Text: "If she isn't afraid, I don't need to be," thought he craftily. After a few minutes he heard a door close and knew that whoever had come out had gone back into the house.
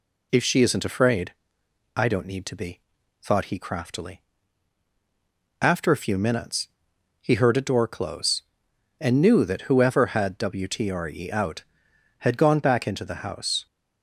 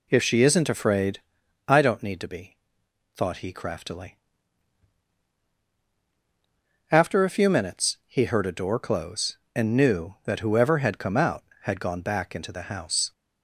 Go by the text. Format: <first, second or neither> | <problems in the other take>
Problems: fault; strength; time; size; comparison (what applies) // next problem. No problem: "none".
second | pauses between "minutes" and "he"; noticeable; at 6.6 s; 0.52 s long // says "wtre" for "come"; at 10.3 s